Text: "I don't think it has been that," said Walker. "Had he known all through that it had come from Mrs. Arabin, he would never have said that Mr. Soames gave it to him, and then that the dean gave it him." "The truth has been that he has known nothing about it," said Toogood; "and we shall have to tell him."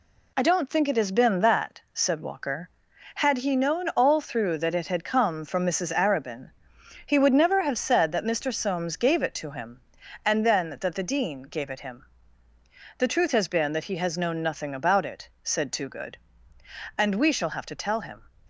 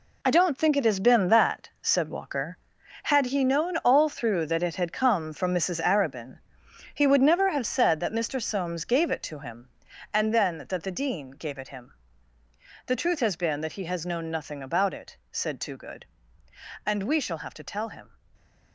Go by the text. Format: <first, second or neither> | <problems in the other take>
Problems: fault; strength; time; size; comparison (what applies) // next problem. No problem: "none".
first | gets quieter; strong; throughout; 10 dB